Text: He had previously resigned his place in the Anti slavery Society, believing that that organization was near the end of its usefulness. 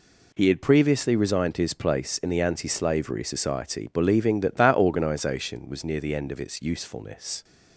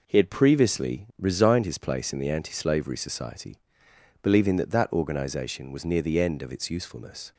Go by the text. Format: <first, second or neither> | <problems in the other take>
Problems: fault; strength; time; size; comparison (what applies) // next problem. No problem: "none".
neither | none